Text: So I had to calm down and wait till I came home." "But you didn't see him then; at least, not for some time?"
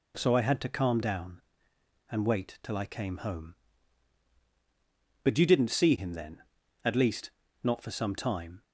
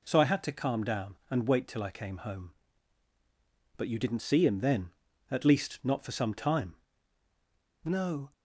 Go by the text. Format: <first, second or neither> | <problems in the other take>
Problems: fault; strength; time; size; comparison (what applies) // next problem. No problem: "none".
first | goes on to say "No"; slight; from 7.8 s on; 0.48 s long